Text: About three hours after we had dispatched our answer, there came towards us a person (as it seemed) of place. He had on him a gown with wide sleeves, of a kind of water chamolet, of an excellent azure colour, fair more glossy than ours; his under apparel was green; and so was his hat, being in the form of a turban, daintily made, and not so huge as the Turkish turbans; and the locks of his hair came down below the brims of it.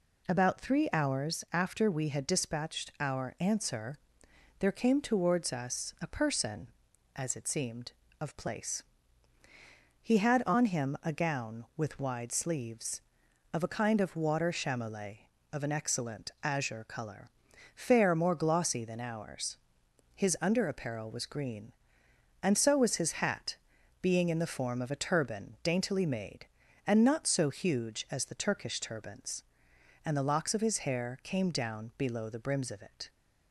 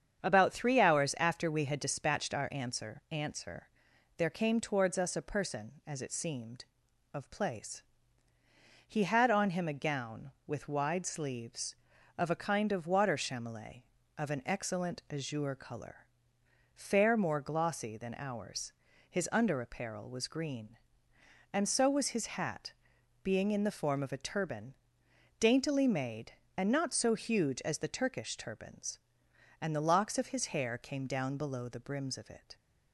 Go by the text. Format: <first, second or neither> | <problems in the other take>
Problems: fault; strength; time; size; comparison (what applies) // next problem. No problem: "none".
first | starts louder than the rest; strong; until 1.2 s; 8 dB // says "answer" twice; at 3.0 s